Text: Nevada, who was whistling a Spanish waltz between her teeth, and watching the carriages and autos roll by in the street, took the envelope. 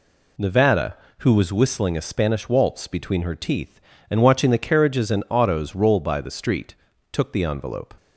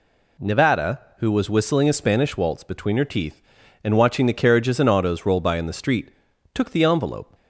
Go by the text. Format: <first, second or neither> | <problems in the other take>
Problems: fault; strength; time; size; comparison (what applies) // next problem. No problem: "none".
second | skips "in"; at 6.2 s